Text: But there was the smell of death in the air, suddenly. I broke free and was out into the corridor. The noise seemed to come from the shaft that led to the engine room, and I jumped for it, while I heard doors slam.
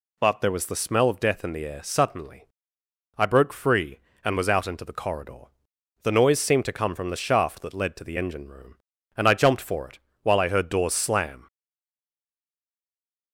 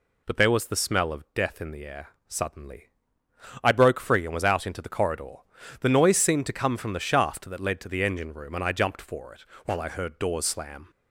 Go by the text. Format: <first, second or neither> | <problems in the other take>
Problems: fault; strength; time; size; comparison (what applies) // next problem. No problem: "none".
second | stays silent after the last word; noticeable; from 11.4 s on; 1.9 s long